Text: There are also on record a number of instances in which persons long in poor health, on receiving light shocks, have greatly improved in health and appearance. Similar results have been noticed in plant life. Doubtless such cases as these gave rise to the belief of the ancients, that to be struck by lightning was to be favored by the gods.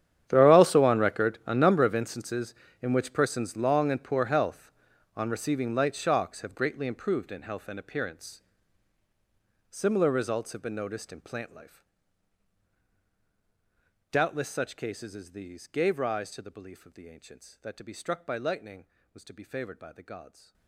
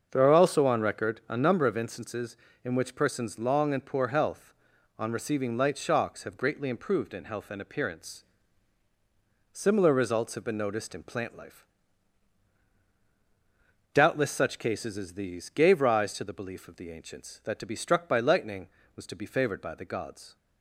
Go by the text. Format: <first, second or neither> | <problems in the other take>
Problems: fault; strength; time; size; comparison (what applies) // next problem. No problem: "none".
second | gets quieter; strong; throughout; 19.5 dB // starts louder than the rest; strong; until 1.3 s; 10 dB; also in the second